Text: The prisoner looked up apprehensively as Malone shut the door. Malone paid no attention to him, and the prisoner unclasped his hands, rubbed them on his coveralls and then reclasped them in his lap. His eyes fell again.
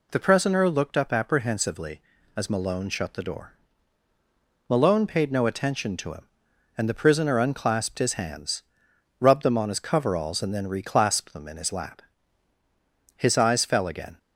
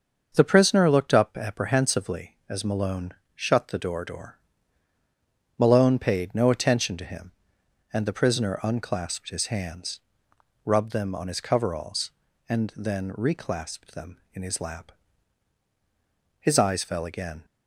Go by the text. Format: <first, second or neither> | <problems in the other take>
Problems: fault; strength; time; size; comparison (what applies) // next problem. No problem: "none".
first | starts louder than the rest; until 1.3 s; 6.5 dB // pauses between "Malone" and "shut"; slight; at 3.1 s; 0.22 s long // says "door" twice; at 4.0 s